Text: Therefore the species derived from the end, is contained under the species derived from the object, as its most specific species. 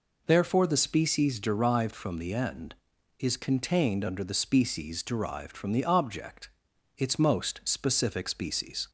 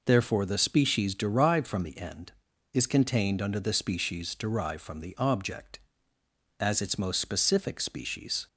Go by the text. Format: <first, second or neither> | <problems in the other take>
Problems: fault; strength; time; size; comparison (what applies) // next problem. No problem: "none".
second | skips "as"; at 6.7 s